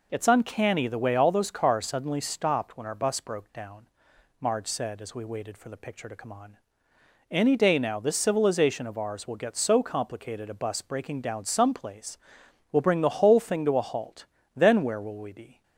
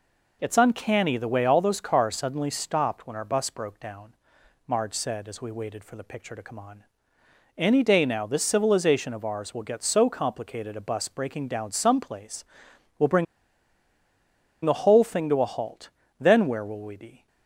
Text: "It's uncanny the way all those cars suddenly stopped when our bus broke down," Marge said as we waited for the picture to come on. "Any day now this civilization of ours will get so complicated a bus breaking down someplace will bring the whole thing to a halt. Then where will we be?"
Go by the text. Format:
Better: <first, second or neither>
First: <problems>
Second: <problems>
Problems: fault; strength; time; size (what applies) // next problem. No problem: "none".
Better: first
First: none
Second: pauses between "bring" and "the"; strong; at 13.2 s; 1.3 s long